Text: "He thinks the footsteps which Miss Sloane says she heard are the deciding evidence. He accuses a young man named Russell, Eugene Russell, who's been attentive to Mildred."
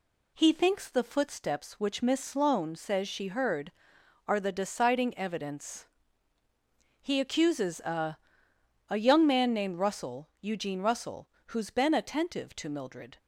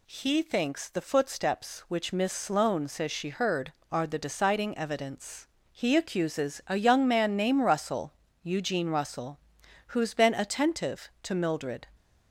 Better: second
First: says "a" twice; at 8.8 s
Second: none

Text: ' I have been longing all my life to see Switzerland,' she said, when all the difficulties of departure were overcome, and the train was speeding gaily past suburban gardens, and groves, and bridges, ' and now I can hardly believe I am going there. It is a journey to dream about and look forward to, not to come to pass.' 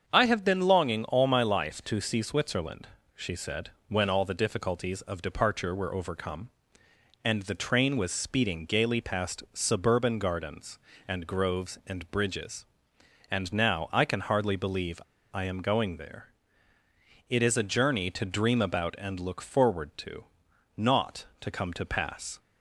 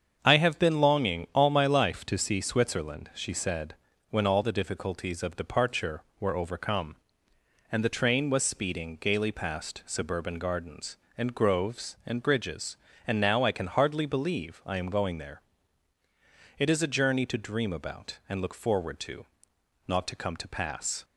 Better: second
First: starts louder than the rest; until 1.1 s; 7 dB // pauses between "believe" and "I"; slight; at 15.0 s; 0.33 s long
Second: starts louder than the rest; strong; until 1.2 s; 7 dB

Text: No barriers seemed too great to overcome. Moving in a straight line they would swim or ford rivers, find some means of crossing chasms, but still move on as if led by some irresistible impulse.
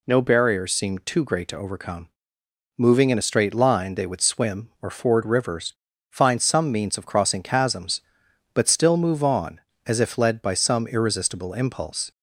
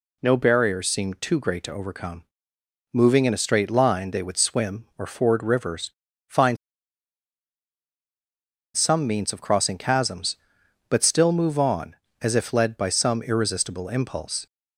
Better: first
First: none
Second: pauses between "find" and "some"; strong; at 6.5 s; 2.1 s long

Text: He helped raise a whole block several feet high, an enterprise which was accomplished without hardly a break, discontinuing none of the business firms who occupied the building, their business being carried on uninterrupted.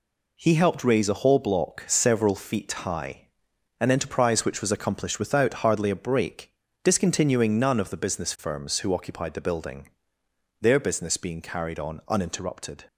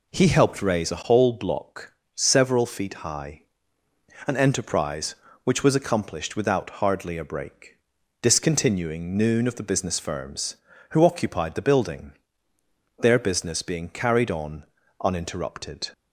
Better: first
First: none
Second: pauses between "block" and "several"; slight; at 1.9 s; 0.22 s long // says "noon" for "none"; at 9.1 s // pauses between "on" and "uninterrupted"; at 14.6 s; 0.40 s long

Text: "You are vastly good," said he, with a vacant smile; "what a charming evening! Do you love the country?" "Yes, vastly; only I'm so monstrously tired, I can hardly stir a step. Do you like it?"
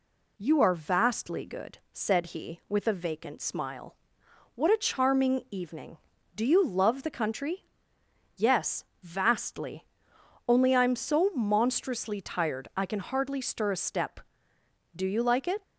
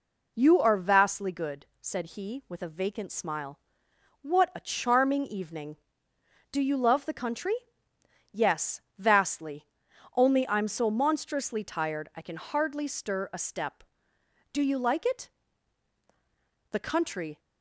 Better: first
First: none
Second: goes on to say "The country"; noticeable; from 16.7 s on; 0.68 s long

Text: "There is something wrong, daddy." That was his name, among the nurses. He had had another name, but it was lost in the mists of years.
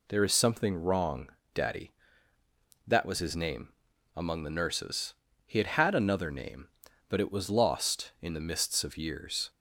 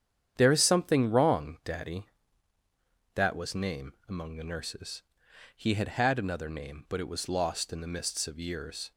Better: first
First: none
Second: starts louder than the rest; strong; until 1.3 s; 9 dB // skips "his"; at 3.5 s

